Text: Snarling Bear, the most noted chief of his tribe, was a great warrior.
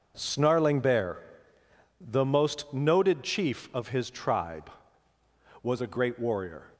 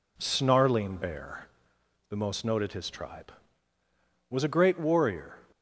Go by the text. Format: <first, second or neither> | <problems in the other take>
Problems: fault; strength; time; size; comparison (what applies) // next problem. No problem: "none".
first | skips "chief of"; at 2.7 s